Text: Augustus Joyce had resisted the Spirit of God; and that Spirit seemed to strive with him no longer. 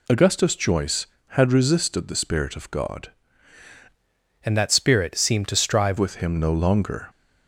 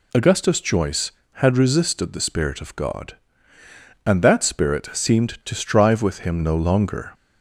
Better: second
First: changes voice from "and" to "strive"; from 4.4 to 5.9 s; 1.5 s long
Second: none

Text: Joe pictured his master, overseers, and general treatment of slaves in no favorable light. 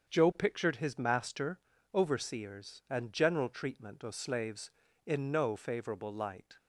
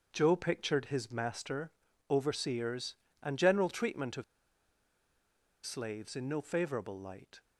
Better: first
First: starts louder than the rest; until 1.1 s; 7 dB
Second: starts louder than the rest; until 1.1 s; 6.5 dB // pauses between "of" and "slaves"; strong; at 4.2 s; 1.4 s long

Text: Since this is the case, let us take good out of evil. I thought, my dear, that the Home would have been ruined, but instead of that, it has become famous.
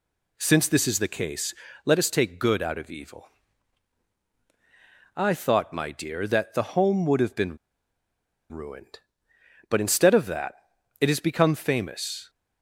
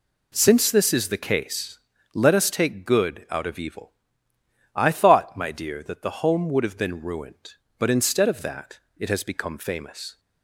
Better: second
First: pauses between "been" and "ruined"; noticeable; at 7.5 s; 0.92 s long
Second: none

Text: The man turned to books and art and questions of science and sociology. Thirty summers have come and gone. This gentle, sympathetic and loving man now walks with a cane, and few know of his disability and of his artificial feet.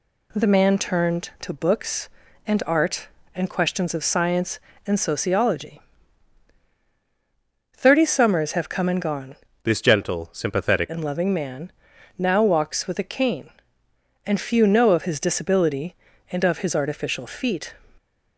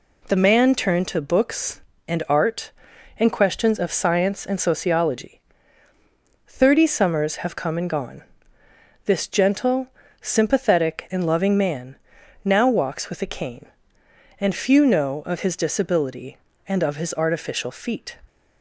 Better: second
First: changes voice from "This" to "sympathetic"; from 9.6 to 10.8 s; 1.2 s long // pauses between "man" and "now"; noticeable; at 11.7 s; 0.48 s long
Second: pauses between "man" and "now"; noticeable; at 11.9 s; 0.50 s long

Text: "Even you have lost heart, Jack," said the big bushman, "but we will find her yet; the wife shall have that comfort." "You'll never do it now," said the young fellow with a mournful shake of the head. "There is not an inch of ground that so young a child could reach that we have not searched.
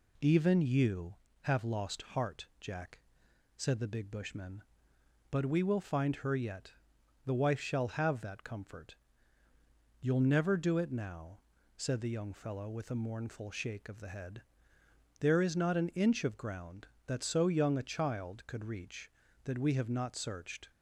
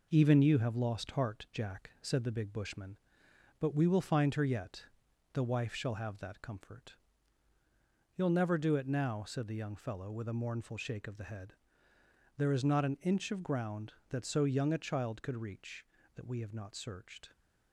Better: first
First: none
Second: gets quieter; noticeable; throughout; 4.5 dB

